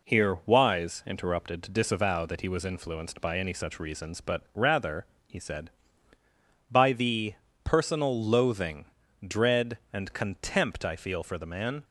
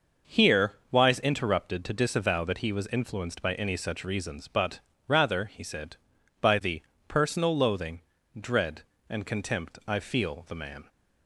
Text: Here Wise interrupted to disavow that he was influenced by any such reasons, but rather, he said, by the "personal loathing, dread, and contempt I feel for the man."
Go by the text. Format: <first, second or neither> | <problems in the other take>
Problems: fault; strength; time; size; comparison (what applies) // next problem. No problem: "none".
first | pauses between "Here" and "Wise"; slight; at 0.7 s; 0.18 s long // pauses between "but" and "rather"; slight; at 4.7 s; 0.28 s long // pauses between "the" and "personal"; slight; at 6.8 s; 0.26 s long; slight in the first // skips "for"; at 10.4 s